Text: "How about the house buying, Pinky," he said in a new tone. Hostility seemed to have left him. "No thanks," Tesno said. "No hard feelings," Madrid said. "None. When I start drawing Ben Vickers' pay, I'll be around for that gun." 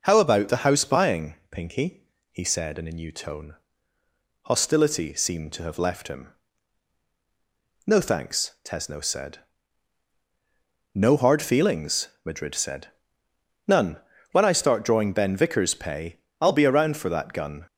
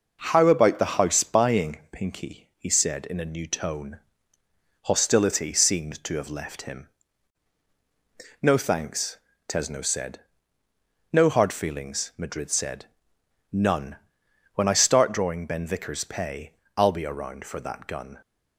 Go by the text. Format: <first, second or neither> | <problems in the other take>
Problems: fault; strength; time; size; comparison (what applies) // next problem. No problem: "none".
neither | none